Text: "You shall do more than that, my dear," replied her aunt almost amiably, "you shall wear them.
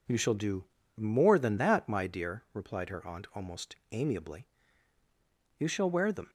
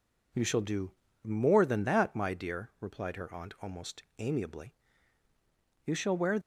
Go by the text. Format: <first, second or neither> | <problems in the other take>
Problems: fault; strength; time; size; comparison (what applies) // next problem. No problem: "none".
first | pauses between "do" and "more"; slight; at 0.9 s; 0.30 s long; slight in the first // pauses between "almost" and "amiably"; slight; at 4.0 s; 0.16 s long; slight in the first // stops before "them"; at 6.4 s